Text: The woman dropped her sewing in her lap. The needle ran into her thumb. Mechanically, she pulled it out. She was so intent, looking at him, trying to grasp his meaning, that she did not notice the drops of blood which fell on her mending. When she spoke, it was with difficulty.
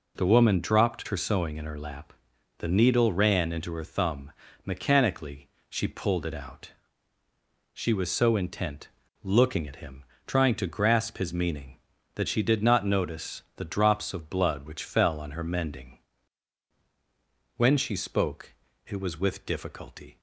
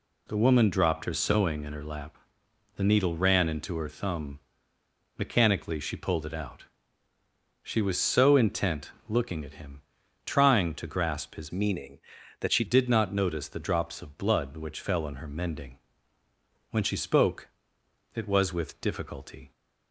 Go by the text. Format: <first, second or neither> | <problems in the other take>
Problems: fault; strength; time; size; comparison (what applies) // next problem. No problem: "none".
first | changes voice from "meaning" to "she"; from 11.5 to 12.6 s; 1.1 s long